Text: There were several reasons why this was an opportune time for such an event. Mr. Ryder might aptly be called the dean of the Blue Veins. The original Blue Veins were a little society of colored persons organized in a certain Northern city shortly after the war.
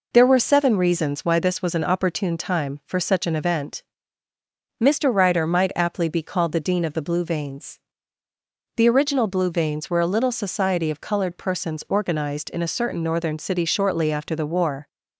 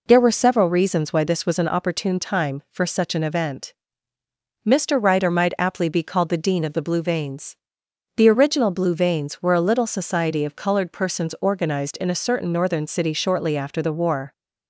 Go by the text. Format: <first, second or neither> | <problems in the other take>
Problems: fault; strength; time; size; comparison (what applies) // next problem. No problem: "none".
second | says "seven" for "several"; at 0.3 s